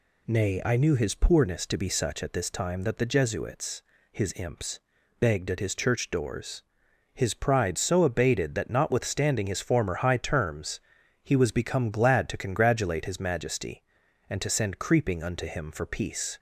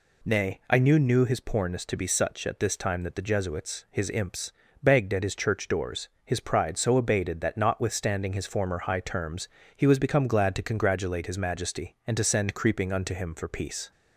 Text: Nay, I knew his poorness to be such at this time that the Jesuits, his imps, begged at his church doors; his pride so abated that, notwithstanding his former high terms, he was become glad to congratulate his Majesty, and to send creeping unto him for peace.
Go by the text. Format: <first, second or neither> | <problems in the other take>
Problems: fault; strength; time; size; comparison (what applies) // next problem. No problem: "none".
first | says "knew" twice; at 1.0 s